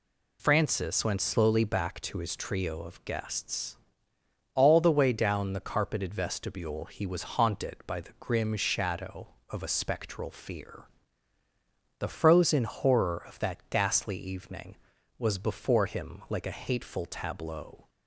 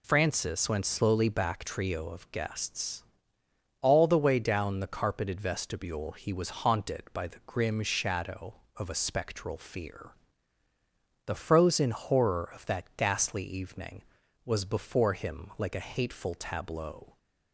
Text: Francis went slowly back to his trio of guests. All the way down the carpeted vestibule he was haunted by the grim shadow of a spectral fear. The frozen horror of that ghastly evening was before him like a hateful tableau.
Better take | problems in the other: first | skips "to his"; at 1.6 s

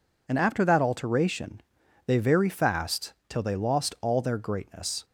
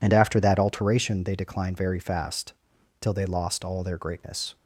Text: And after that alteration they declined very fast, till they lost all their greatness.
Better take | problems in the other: second | pauses between "alteration" and "they"; noticeable; at 1.6 s; 0.46 s long // skips "declined"; at 2.1 s

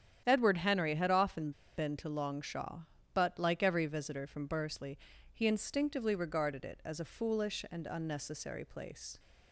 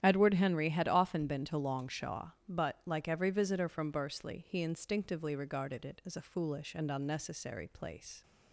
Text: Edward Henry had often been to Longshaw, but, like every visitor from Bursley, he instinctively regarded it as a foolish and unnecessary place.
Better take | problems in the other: second | starts louder than the rest; strong; until 1.2 s; 10 dB; strong in the second // pauses between "often" and "been"; slight; at 1.5 s; 0.26 s long

